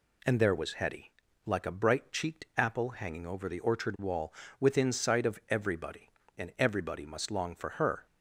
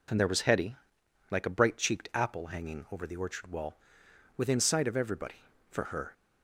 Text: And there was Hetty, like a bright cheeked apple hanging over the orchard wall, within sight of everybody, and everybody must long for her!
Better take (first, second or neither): first